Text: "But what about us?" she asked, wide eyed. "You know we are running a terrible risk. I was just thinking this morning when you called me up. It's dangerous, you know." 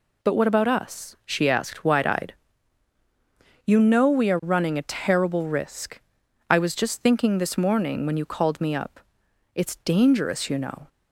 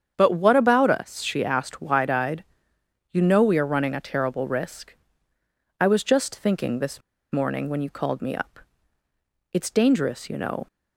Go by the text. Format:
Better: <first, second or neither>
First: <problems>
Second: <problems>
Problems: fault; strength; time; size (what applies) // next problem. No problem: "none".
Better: first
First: none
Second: starts louder than the rest; strong; until 1.1 s; 8 dB // pauses between "this" and "morning"; slight; at 7.0 s; 0.31 s long